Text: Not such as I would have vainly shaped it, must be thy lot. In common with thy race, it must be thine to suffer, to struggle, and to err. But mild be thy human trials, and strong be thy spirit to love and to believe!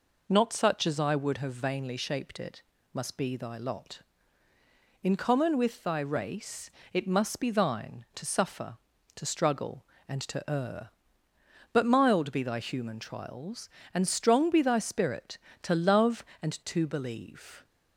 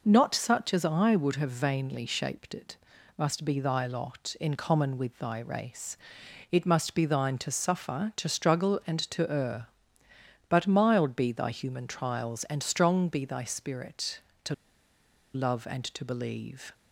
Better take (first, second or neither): first